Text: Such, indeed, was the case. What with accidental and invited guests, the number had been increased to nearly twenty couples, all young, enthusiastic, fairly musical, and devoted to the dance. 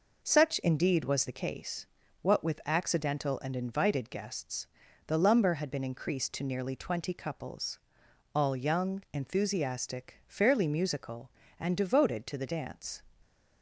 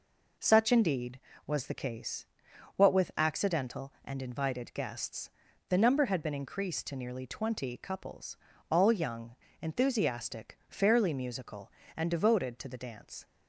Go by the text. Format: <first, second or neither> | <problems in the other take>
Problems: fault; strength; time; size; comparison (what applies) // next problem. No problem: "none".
second | says "lumber" for "number"; at 5.1 s